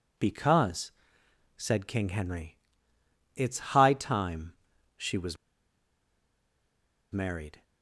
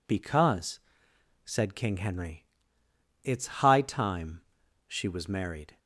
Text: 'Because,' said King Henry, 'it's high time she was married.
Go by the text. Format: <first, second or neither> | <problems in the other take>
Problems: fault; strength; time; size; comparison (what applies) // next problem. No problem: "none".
second | pauses between "time" and "she"; at 4.5 s; 0.42 s long; also in the second // pauses between "was" and "married"; strong; at 5.3 s; 1.7 s long